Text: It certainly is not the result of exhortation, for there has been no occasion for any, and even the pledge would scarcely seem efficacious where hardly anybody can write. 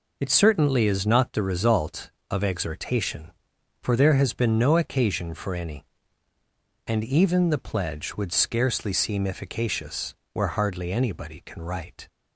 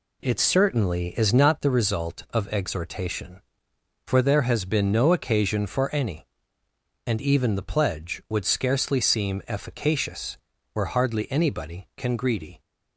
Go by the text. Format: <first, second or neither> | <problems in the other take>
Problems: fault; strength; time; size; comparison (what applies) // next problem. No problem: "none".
first | pauses between "efficacious" and "where"; at 10.3 s; 0.38 s long; slight in the first // says "greedy" for "write"; at 12.1 s